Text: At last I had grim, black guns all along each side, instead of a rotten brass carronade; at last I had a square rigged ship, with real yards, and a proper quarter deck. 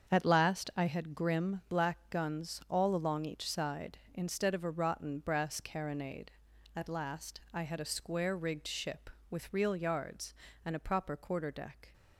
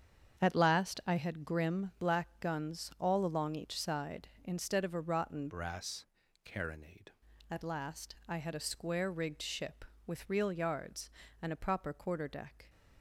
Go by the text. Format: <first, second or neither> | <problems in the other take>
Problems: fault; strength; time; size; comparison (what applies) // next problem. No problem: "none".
first | starts louder than the rest; strong; until 1.4 s; 7.5 dB; strong in the first // changes voice from "brass" to "carronade"; from 5.4 to 7.0 s; 1.6 s long // pauses between "brass" and "carronade"; at 6.0 s; 0.40 s long